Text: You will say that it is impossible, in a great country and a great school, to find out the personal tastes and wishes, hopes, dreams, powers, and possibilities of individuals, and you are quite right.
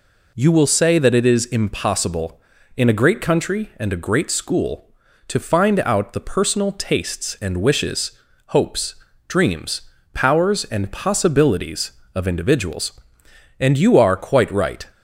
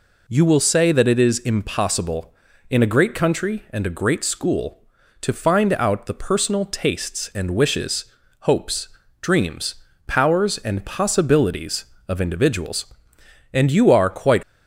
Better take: first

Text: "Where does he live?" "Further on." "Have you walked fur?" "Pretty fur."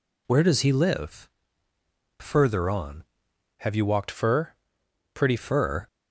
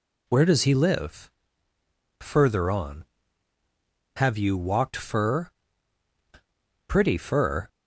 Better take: second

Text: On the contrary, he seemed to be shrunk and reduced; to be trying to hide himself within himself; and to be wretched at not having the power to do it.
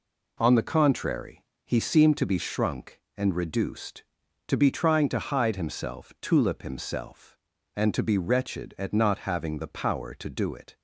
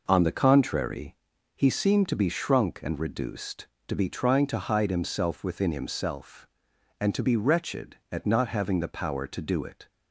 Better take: second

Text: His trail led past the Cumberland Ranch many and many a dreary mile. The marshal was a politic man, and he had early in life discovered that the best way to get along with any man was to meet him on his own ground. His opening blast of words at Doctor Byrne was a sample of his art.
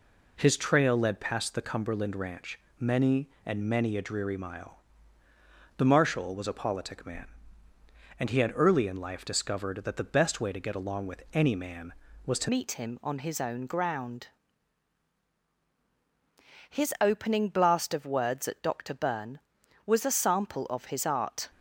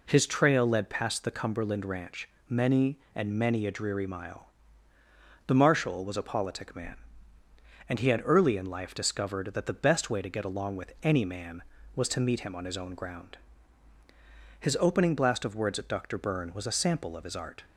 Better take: second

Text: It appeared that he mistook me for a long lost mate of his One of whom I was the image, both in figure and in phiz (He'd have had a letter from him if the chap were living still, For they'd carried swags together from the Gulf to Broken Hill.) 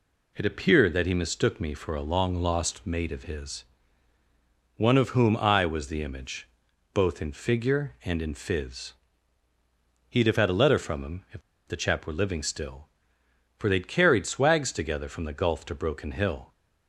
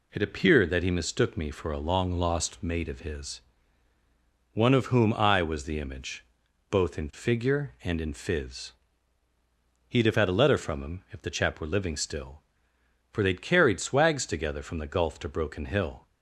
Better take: second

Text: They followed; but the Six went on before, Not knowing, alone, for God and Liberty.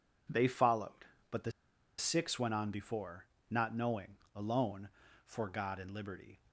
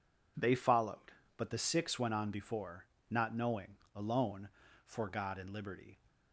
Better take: second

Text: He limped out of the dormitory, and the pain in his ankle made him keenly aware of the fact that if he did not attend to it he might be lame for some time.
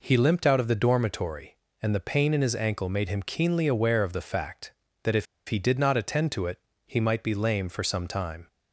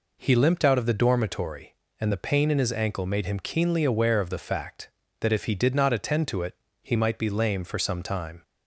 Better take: second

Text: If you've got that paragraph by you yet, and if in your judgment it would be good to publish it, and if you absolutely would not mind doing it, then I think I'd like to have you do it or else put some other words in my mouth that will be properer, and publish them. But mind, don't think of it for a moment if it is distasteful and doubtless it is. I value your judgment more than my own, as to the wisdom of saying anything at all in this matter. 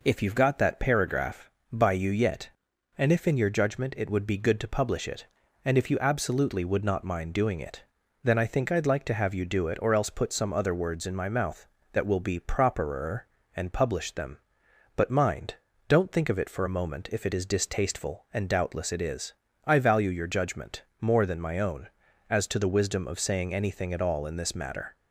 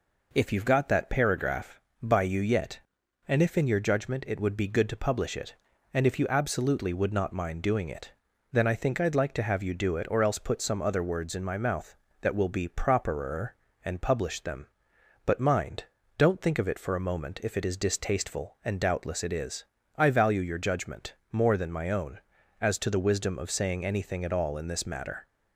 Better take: neither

